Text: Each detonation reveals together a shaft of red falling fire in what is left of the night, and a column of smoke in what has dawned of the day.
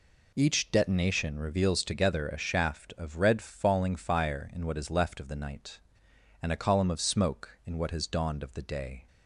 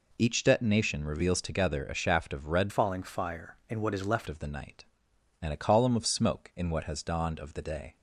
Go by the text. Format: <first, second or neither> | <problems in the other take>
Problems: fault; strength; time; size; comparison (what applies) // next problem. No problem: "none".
first | changes voice from "falling" to "left"; from 2.6 to 4.2 s; 1.6 s long